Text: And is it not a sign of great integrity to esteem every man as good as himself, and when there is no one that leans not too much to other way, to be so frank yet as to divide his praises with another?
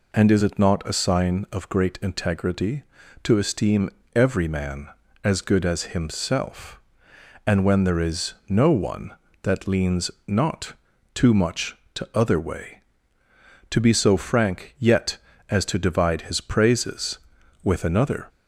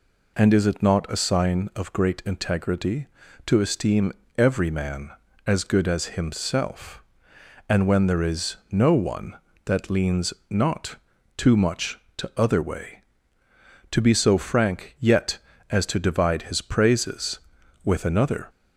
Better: neither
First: pauses between "esteem" and "every"; slight; at 3.9 s; 0.24 s long // pauses between "leans" and "not"; slight; at 10.1 s; 0.16 s long // pauses between "not" and "too"; at 10.7 s; 0.42 s long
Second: pauses between "esteem" and "every"; slight; at 4.1 s; 0.24 s long // pauses between "leans" and "not"; slight; at 10.3 s; 0.16 s long // pauses between "not" and "too"; at 10.9 s; 0.42 s long

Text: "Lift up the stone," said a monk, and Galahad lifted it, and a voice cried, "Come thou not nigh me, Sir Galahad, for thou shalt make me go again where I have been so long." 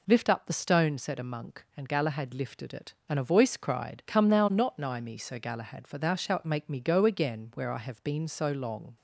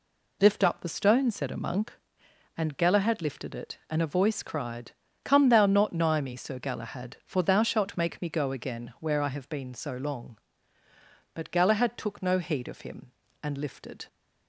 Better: first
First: none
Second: goes on to say "But Galahad took no heed of him and lifted"; strong; from 11.3 s on; 2.7 s long

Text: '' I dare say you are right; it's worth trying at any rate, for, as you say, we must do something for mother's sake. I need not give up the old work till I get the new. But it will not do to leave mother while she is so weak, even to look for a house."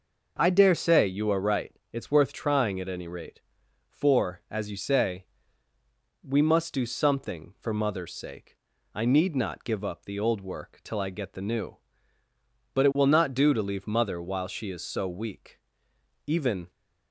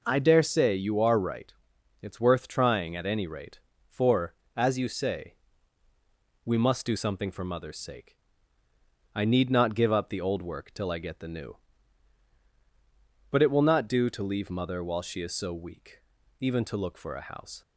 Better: second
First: stops before "to look for a house"; at 16.6 s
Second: none

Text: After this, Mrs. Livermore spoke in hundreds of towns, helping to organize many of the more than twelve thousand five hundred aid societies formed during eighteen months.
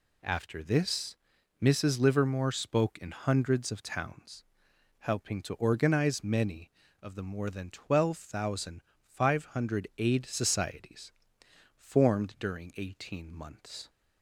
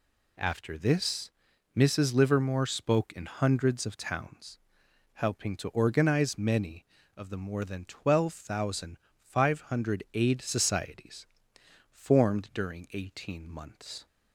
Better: neither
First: pauses between "thousand" and "five"; slight; at 8.8 s; 0.24 s long // pauses between "societies" and "formed"; noticeable; at 11.1 s; 0.66 s long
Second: pauses between "thousand" and "five"; slight; at 8.9 s; 0.24 s long // pauses between "societies" and "formed"; noticeable; at 11.2 s; 0.66 s long

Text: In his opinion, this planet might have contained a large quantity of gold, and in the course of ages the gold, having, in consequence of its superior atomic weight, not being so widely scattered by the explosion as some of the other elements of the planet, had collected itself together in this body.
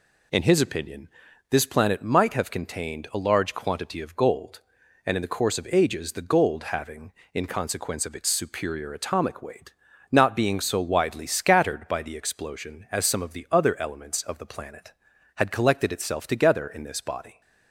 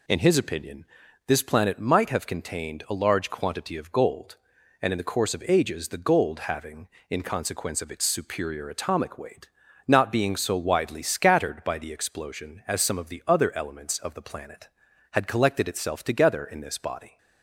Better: neither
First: none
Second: none

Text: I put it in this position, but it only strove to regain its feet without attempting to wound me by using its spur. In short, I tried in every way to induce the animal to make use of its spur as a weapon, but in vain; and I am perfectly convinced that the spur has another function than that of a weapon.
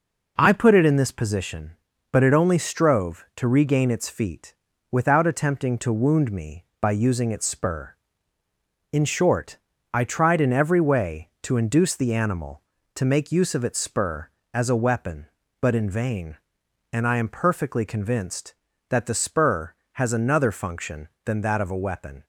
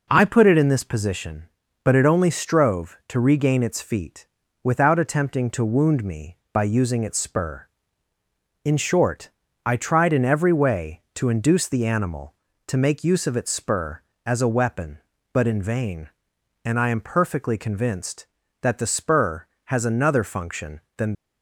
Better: first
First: pauses between "feet" and "without"; at 4.5 s; 0.38 s long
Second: pauses between "feet" and "without"; at 4.2 s; 0.38 s long // stops before "that of a weapon"; at 21.1 s

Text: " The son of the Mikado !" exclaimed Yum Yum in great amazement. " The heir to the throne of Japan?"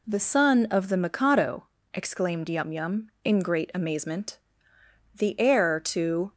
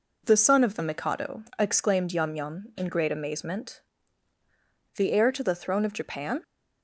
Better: second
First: stops before "the throne of Japan"; at 6.3 s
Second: none

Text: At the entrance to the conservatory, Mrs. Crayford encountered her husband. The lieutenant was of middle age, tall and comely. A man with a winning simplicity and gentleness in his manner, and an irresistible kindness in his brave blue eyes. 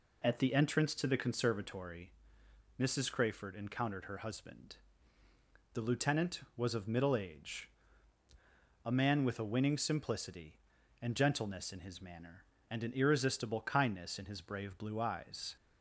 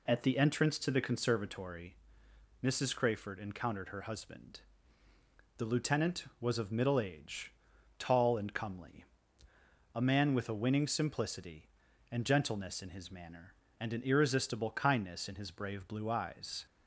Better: second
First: skips "tall and comely"; at 8.2 s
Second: none

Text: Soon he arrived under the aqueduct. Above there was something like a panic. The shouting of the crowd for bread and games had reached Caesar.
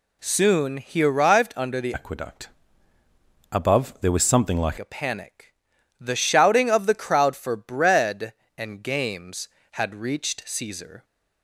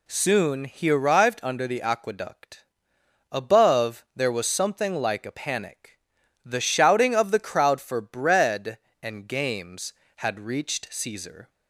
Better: second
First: changes voice from "aqueduct" to "like"; from 1.9 to 4.7 s; 2.8 s long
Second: none

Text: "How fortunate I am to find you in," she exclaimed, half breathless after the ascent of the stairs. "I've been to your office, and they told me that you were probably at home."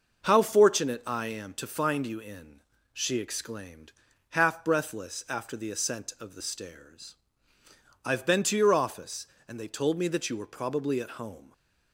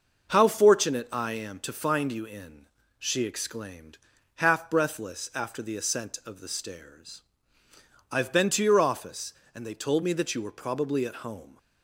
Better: neither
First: none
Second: none

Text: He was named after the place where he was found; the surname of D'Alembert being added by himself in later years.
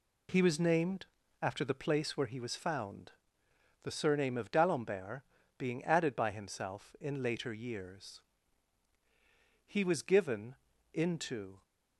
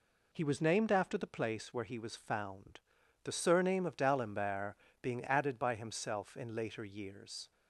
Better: second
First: pauses between "named" and "after"; slight; at 1.0 s; 0.36 s long // pauses between "D'Alembert" and "being"; slight; at 5.2 s; 0.36 s long // goes on to say "He was given into"; strong; from 9.6 s on; 1.9 s long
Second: pauses between "D'Alembert" and "being"; slight; at 4.7 s; 0.28 s long

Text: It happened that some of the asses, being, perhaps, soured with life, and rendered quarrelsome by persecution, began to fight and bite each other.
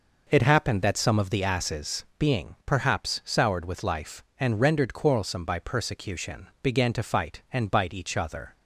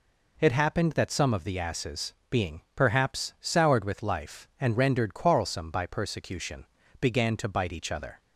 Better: first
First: none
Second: skips "fight and"; at 7.4 s

